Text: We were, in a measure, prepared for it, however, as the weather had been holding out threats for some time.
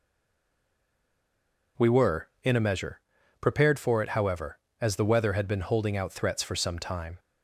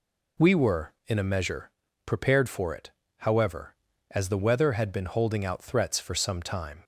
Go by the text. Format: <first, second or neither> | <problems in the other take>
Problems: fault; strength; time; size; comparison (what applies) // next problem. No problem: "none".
second | stays silent before the first word; noticeable; until 1.7 s; 1.7 s long